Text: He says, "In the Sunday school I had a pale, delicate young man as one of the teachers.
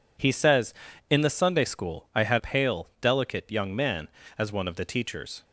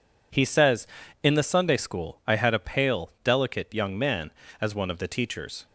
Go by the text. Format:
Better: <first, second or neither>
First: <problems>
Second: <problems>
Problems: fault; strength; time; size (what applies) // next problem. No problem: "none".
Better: second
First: skips "a"; at 2.3 s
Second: none